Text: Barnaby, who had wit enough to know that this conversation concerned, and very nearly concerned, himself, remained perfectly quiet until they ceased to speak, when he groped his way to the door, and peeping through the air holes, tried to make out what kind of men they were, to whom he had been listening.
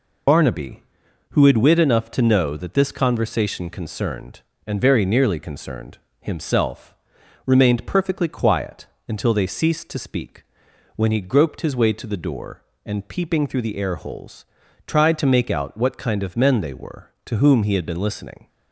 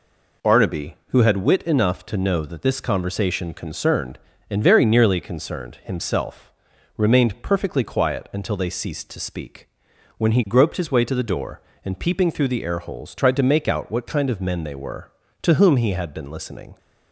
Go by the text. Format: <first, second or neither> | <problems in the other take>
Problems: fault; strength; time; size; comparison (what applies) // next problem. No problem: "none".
second | loses the start of "Barnaby"; at 0.2 s; 135 ms // pauses between "quiet" and "until"; slight; at 8.8 s; 0.22 s long